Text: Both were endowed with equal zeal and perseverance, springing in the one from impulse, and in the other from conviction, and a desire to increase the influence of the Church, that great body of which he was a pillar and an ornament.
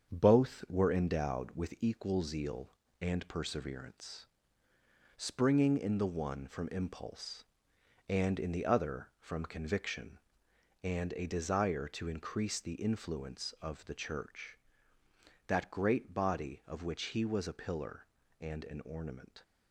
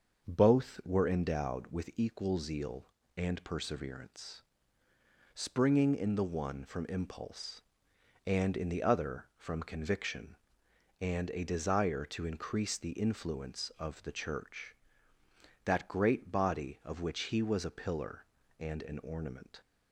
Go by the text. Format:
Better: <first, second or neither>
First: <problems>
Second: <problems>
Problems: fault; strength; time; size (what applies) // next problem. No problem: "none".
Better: second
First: gets quieter; noticeable; throughout; 5 dB // starts louder than the rest; strong; until 1.1 s; 7 dB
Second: starts louder than the rest; until 1.3 s; 6.5 dB